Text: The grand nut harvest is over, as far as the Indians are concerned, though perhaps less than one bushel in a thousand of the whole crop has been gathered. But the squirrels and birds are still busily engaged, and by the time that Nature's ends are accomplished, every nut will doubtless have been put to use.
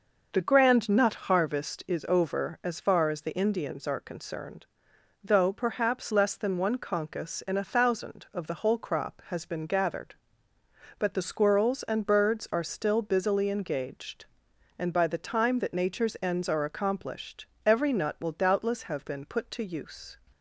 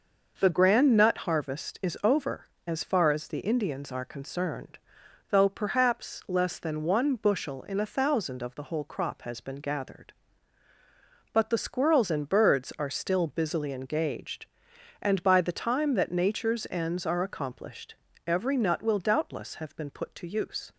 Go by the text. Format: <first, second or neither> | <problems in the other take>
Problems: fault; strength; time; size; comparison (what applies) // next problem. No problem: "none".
second | says "concus" for "bushel"; at 6.7 s